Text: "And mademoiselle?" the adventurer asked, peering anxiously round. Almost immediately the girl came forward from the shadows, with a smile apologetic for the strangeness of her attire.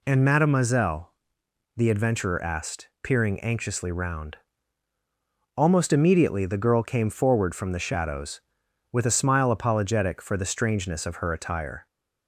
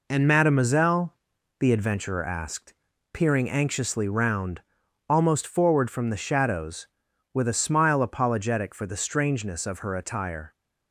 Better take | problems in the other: first | skips "immediately the girl came"; at 5.4 s

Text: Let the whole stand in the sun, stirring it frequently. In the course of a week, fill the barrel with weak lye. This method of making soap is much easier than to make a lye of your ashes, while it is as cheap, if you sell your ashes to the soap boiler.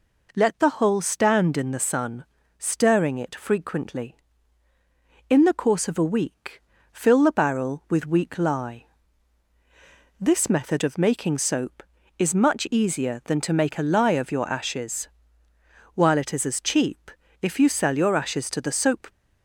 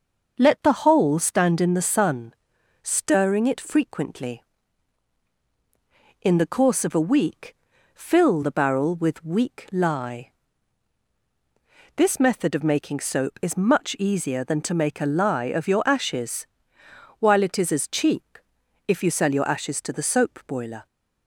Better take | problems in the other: second | stops before "boiler"; at 19.0 s

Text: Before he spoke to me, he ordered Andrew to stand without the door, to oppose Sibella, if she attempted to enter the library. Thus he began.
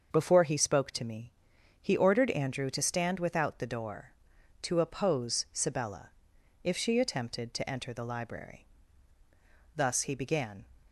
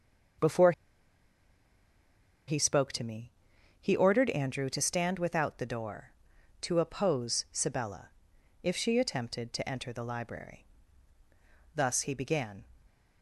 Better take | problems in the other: first | starts louder than the rest; until 3.1 s; 6.5 dB; also in the first // pauses between "Before" and "he"; strong; at 0.7 s; 1.7 s long

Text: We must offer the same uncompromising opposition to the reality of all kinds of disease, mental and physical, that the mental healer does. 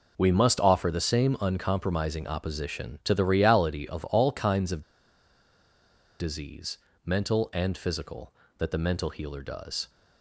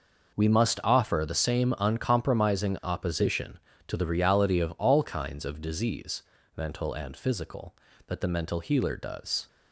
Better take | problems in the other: second | pauses between "of" and "disease"; strong; at 4.8 s; 1.3 s long

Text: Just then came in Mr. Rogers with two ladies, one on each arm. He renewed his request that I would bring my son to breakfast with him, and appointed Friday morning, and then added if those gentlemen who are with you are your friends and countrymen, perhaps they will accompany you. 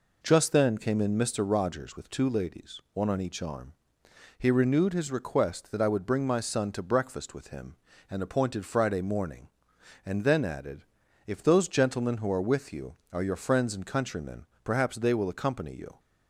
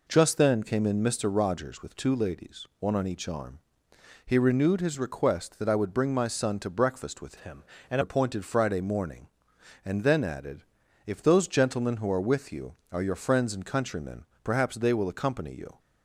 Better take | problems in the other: first | changes voice from "him" to "and"; from 7.3 to 7.9 s; 0.6 s long // pauses between "added" and "if"; at 10.6 s; 0.44 s long; also in the first

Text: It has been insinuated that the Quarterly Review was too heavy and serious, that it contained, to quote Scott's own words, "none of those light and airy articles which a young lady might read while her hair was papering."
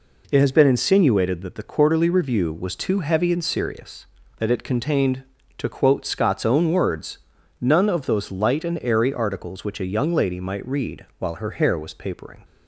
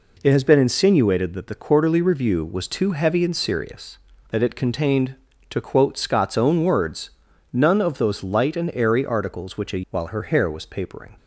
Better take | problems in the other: first | skips "young lady might read"; at 9.8 s

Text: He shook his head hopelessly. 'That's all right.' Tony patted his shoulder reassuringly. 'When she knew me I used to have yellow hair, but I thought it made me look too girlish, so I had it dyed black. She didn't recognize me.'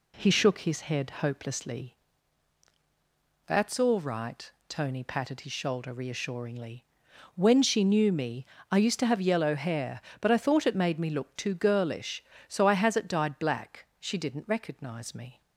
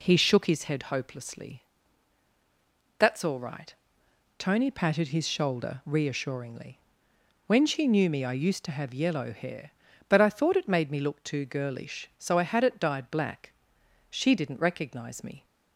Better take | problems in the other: second | pauses between "me" and "I"; slight; at 8.4 s; 0.26 s long // says "has" for "had"; at 12.7 s

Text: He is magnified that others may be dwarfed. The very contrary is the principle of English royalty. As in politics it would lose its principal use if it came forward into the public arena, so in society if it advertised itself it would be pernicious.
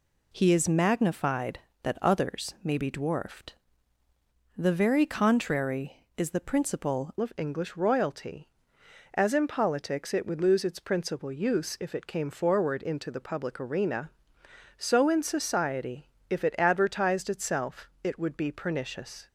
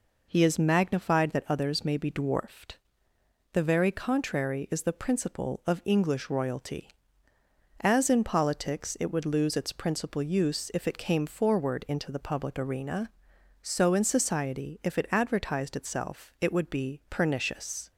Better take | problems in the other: second | changes voice at "of"; from 7.2 s on; 12.0 s long // pauses between "society" and "if"; slight; at 16.0 s; 0.22 s long // pauses between "itself" and "it"; slight; at 17.8 s; 0.16 s long

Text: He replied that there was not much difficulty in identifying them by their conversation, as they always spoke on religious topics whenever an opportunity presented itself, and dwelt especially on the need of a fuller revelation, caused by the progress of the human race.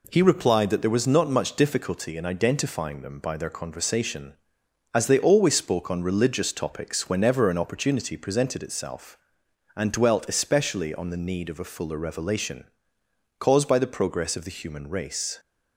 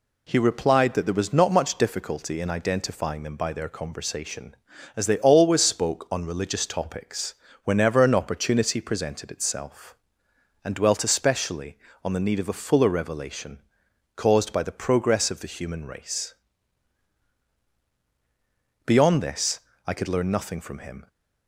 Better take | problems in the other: first | pauses between "topics" and "whenever"; slight; at 7.3 s; 0.30 s long // goes on to say "Beyond this I could learn nothing from him"; strong; from 18.8 s on; 2.2 s long

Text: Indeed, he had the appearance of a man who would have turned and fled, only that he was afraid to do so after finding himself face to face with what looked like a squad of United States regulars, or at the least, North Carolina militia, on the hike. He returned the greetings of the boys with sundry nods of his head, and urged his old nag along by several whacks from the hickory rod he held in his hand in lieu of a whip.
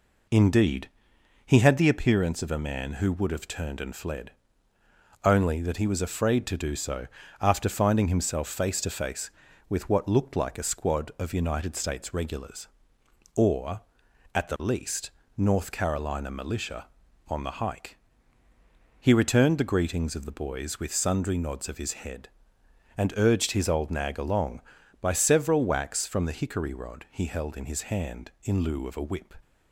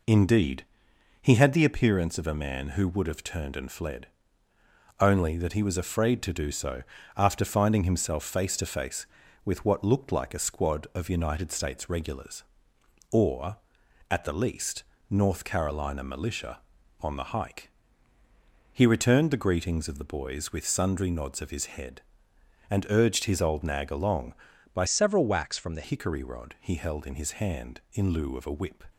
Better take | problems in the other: first | pauses between "so" and "after"; slight; at 6.8 s; 0.34 s long; slight in the first // changes voice from "several" to "the"; from 24.8 to 25.8 s; 1.0 s long

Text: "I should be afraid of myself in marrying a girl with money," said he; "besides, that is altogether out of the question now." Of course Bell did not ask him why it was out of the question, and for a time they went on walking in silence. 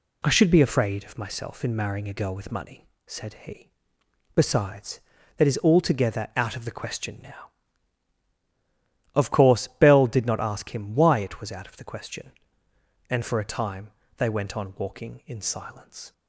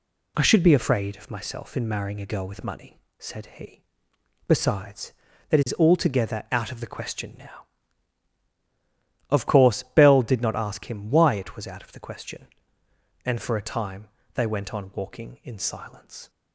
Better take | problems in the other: neither | pauses between "time" and "they"; slight; the same in both

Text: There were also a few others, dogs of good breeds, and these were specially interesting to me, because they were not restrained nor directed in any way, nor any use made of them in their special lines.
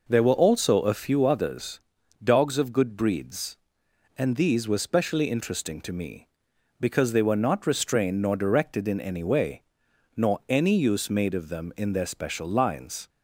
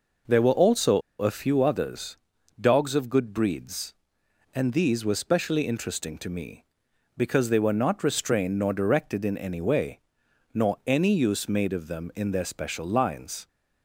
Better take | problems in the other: first | pauses between "also" and "a"; slight; at 0.9 s; 0.20 s long

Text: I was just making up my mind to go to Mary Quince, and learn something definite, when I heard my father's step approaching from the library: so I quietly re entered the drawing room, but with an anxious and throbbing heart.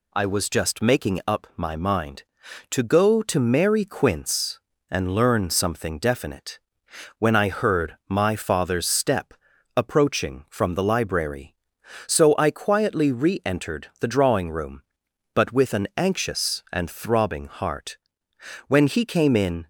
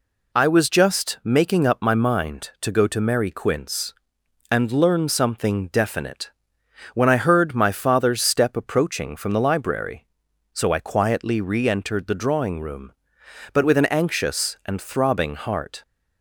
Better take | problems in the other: second | pauses between "step" and "approaching"; at 9.3 s; 0.42 s long // goes on to say "When he came in"; noticeable; from 18.6 s on; 1.0 s long

